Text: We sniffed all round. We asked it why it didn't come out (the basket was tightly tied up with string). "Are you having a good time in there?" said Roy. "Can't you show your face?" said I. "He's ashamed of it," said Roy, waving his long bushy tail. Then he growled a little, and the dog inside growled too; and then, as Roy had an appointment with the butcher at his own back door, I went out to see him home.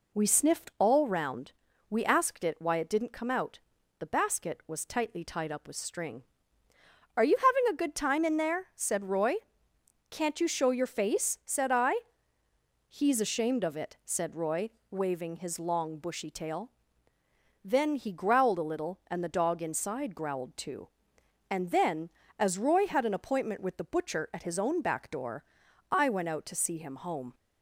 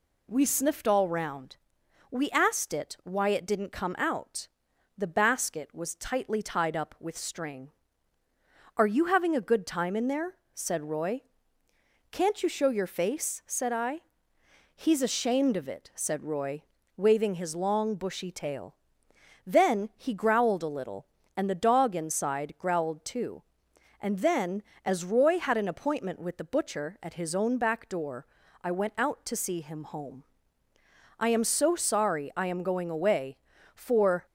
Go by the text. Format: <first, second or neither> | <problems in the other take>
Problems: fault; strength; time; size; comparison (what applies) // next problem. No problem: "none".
first | goes on to say "I am so sorry I am going away for"; strong; from 31.1 s on; 3.0 s long